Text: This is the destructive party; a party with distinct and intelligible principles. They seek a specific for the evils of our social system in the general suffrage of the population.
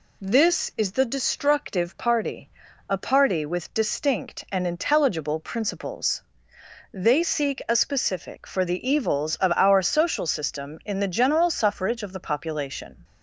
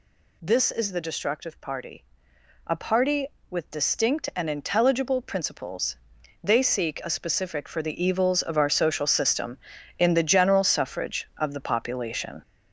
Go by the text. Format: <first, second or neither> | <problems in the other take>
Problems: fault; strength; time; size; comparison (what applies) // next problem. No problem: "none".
first | gets louder; noticeable; throughout; 5.5 dB